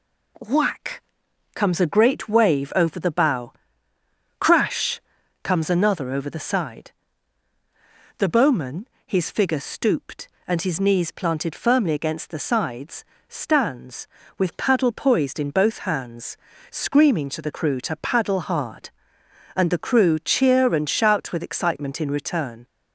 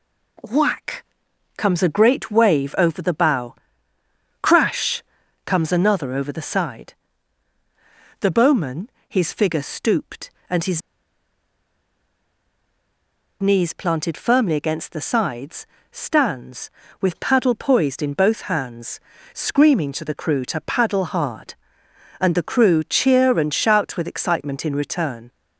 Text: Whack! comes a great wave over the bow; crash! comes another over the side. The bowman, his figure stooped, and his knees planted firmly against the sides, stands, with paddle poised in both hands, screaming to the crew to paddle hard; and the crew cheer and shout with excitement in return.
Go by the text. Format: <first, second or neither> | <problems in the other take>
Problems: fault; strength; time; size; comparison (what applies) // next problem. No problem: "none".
first | pauses between "his" and "knees"; strong; at 10.8 s; 2.6 s long